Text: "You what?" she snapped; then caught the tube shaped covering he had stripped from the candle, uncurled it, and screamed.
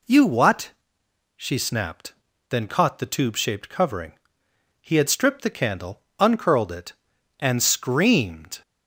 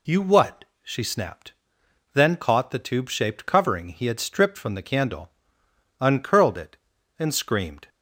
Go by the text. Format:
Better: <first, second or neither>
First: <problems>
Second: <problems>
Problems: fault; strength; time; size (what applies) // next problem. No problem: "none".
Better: second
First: pauses between "covering" and "he"; noticeable; at 4.1 s; 0.64 s long // skips "from"; at 5.4 s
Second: none